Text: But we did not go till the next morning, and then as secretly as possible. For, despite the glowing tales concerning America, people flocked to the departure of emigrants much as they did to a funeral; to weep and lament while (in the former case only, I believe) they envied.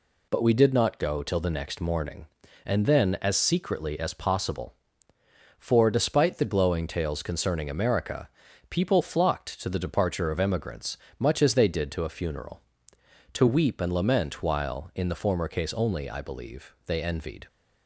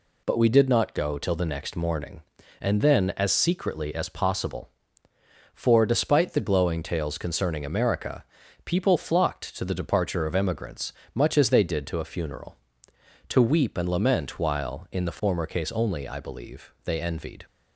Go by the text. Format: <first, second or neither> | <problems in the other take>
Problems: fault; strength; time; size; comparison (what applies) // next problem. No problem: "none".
neither | pauses between "emigrants" and "much"; slight; the same in both